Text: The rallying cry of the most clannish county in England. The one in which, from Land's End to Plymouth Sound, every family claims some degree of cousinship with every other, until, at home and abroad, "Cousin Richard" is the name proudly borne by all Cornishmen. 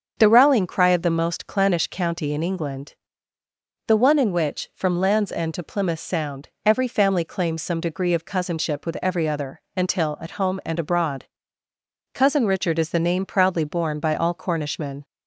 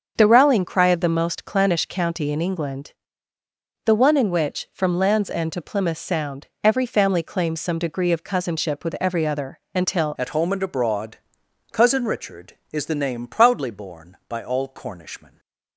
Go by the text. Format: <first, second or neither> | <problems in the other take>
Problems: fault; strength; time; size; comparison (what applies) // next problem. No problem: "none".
first | starts louder than the rest; until 1.1 s; 6.5 dB; also in the first // changes voice at "at"; from 10.1 s on; 5.2 s long